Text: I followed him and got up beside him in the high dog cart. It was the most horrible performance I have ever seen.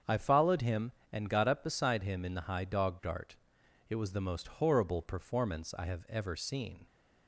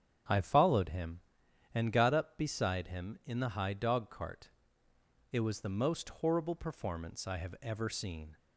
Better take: second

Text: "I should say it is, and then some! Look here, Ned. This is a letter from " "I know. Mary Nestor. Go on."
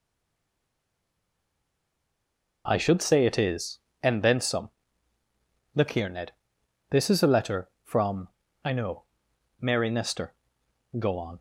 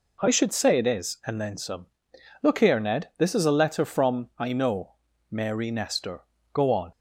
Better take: second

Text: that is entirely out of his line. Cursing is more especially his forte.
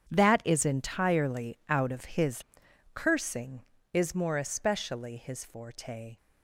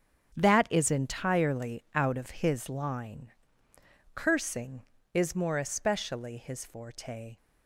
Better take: second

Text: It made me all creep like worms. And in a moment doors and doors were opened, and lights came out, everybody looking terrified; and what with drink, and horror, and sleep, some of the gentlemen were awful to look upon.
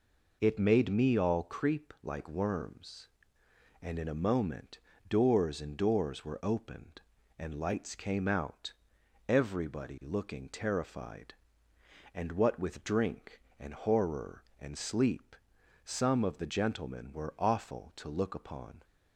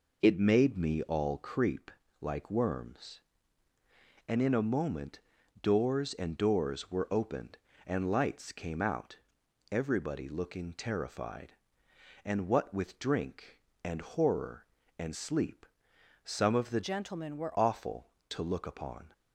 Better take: first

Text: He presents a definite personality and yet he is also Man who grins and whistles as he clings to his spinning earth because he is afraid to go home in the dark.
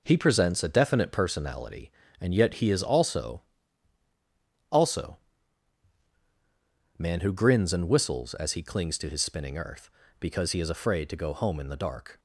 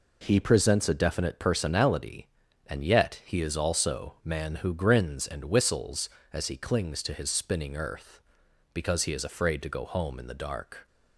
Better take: second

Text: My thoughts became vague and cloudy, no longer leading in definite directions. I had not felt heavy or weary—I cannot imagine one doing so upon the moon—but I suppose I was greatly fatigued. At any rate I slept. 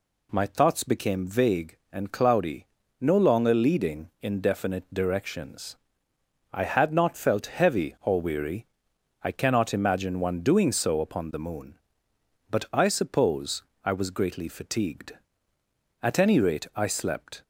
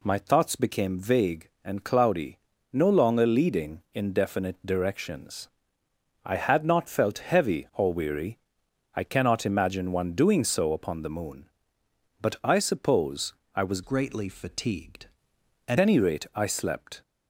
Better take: first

